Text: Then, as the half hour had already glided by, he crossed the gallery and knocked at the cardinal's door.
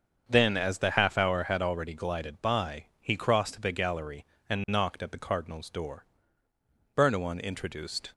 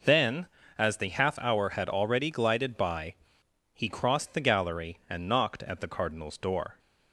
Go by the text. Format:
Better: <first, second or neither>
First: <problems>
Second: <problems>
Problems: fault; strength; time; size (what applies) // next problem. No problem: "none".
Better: second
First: starts louder than the rest; until 1.2 s; 7 dB // goes on to say "Bernouin introduced"; noticeable; from 6.9 s on; 1.1 s long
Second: none